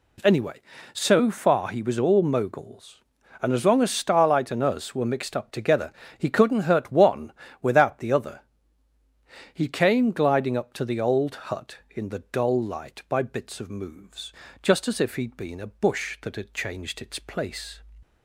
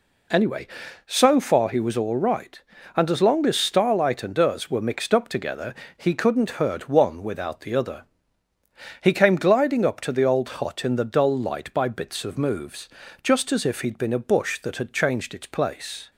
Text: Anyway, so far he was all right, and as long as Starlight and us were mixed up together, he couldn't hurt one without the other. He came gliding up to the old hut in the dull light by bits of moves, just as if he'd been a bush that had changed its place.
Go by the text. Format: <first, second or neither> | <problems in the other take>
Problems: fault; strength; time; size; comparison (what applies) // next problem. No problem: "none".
second | says "moguls" for "right"; at 2.2 s // pauses between "one" and "without"; slight; at 7.3 s; 0.30 s long